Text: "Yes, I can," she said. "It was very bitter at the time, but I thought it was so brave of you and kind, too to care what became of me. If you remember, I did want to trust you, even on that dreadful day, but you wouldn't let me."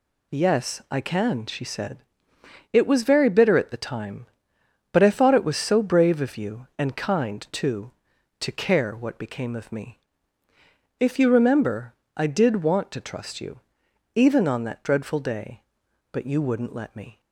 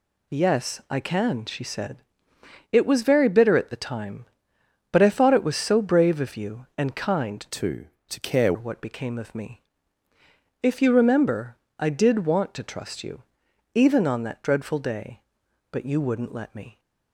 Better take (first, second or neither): first